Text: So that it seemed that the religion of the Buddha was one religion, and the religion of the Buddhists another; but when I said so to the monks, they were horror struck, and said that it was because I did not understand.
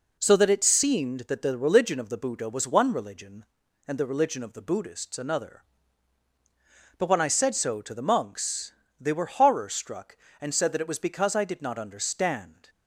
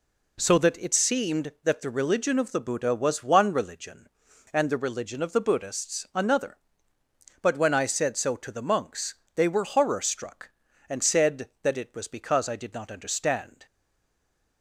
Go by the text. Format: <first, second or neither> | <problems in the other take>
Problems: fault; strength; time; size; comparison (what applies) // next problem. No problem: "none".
first | stays silent after the last word; slight; from 13.6 s on; 1.0 s long